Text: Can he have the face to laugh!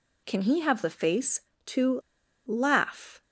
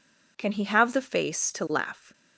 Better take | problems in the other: second | pauses between "to" and "laugh"; noticeable; at 1.9 s; 0.47 s long

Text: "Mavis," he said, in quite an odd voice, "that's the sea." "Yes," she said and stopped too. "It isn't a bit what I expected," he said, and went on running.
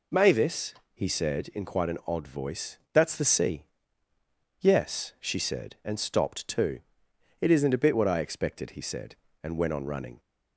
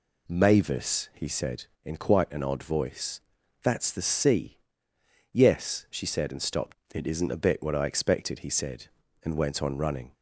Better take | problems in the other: first | skips "too"; at 6.8 s

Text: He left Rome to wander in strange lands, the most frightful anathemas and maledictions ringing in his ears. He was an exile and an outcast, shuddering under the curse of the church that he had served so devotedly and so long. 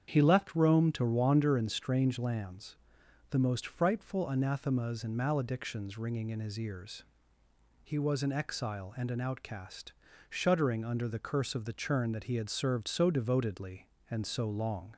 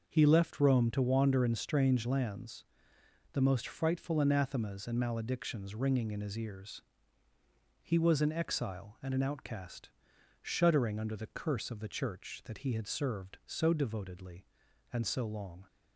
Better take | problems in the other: second | starts louder than the rest; strong; until 1.1 s; 8 dB // says "churn" for "church"; at 11.7 s

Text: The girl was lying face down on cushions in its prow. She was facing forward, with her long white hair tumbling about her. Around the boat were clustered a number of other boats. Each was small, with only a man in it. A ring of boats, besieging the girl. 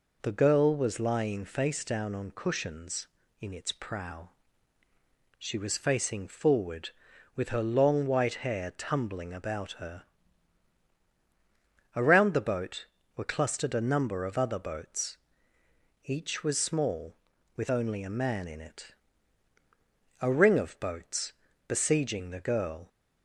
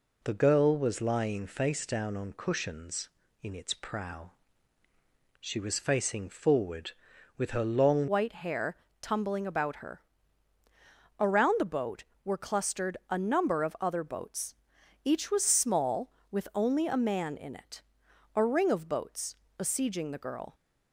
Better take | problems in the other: first | changes voice at "white"; from 8.0 s on; 12.5 s long // pauses between "hair" and "tumbling"; slight; at 8.7 s; 0.24 s long

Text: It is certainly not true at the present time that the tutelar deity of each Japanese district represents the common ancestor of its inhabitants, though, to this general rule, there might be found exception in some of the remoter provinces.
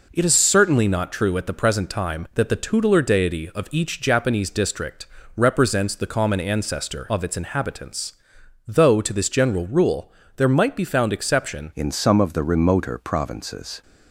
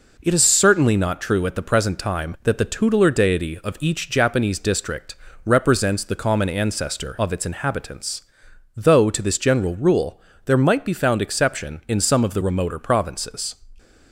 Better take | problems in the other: second | pauses between "district" and "represents"; slight; at 5.0 s; 0.30 s long; slight in the second // changes voice at "in"; from 11.7 s on; 2.1 s long

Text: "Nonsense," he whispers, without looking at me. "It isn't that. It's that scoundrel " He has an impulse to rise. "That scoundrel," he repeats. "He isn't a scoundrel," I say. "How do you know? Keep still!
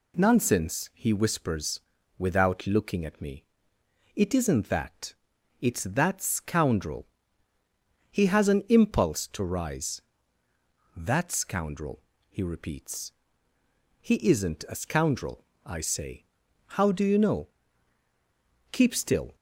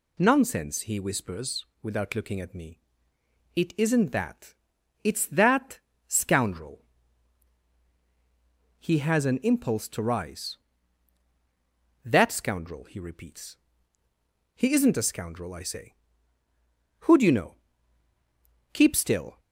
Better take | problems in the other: first | pauses between "that" and "scoundrel"; slight; at 5.7 s; 0.28 s long // says "Who" for "How"; at 17.0 s

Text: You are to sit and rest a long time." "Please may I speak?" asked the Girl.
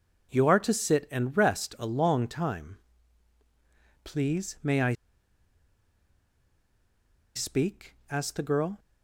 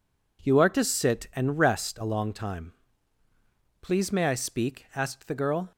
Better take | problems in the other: second | pauses between "I" and "speak"; strong; at 4.9 s; 2.4 s long

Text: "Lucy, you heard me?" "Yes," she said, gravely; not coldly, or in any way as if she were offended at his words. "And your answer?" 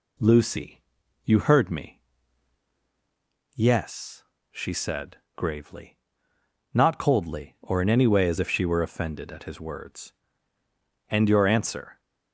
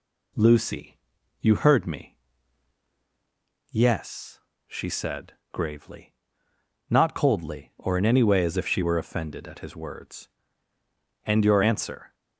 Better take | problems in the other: neither | none

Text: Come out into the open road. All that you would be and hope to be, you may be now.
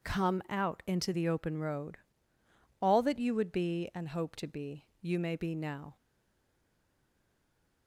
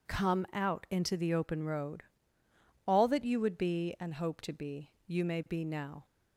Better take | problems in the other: second | stays silent after the last word; noticeable; from 5.9 s on; 1.9 s long

